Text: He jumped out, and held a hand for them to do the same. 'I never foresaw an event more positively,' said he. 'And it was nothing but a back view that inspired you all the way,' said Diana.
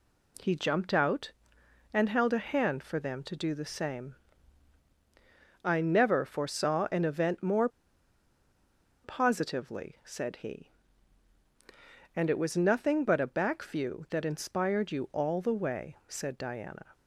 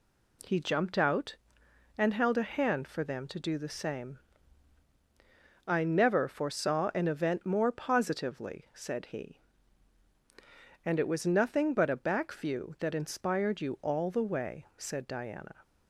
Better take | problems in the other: second | pauses between "more" and "positively"; strong; at 7.6 s; 1.3 s long

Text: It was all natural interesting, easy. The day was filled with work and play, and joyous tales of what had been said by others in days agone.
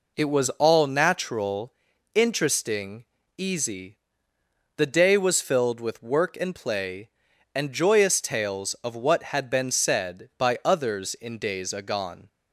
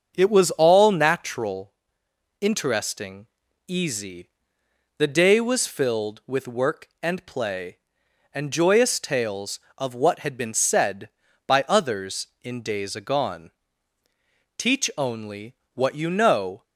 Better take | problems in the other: first | starts louder than the rest; until 1.1 s; 6.5 dB // pauses between "natural" and "interesting"; noticeable; at 1.7 s; 0.70 s long; also in the first // goes on to say "Teach only what you know"; strong; from 14.5 s on; 2.0 s long

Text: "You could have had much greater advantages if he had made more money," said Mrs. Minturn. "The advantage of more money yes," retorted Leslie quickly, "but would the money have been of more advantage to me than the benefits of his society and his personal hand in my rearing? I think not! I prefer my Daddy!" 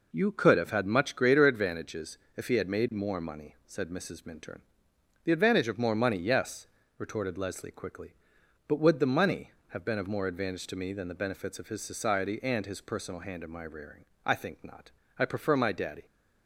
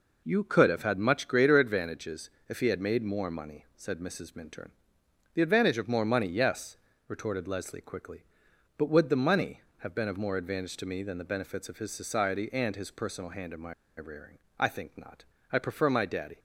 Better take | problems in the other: first | pauses between "advantages" and "if"; slight; at 2.2 s; 0.20 s long; slight in the first // pauses between "my" and "rearing"; slight; at 13.7 s; 0.25 s long

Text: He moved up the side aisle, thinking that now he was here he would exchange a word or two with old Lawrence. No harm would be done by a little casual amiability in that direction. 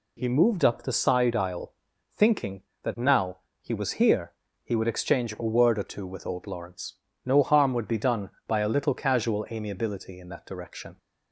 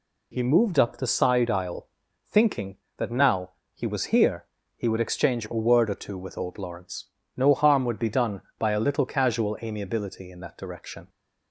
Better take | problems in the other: neither | pauses between "now" and "he"; slight; the same in both // pauses between "here" and "he"; slight; the same in both

